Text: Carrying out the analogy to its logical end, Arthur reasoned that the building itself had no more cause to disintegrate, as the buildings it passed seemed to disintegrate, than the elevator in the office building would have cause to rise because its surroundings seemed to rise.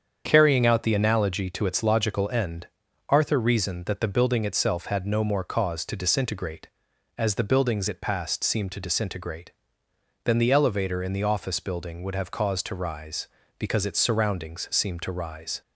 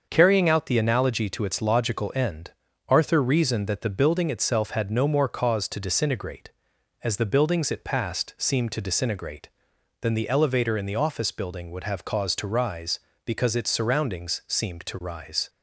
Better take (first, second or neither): neither